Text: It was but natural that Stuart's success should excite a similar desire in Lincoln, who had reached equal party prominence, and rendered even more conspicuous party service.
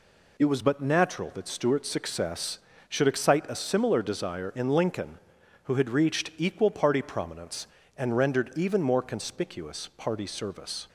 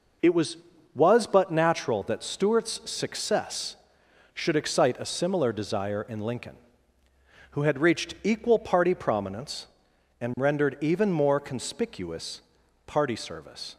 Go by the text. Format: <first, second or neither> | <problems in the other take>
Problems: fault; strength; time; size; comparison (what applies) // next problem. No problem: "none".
first | says "was" twice; at 0.9 s // pauses between "conspicuous" and "party"; noticeable; at 12.4 s; 0.46 s long